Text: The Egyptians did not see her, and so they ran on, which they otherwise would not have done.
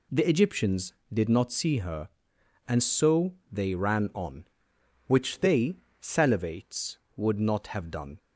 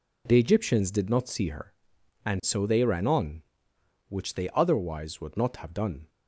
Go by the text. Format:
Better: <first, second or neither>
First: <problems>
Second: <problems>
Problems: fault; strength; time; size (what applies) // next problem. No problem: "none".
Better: second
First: pauses between "so" and "they"; slight; at 3.3 s; 0.18 s long // says "salivates" for "otherwise"; at 5.9 s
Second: none